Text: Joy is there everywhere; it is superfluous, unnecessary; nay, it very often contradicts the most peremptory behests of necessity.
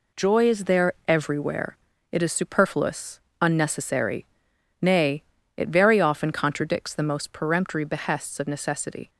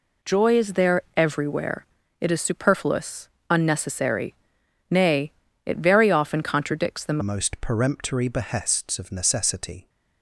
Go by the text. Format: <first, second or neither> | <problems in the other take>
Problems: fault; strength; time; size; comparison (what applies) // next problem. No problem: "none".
first | pauses between "there" and "everywhere"; slight; at 1.0 s; 0.16 s long; slight in the first // changes voice at "most"; from 7.2 s on; 2.6 s long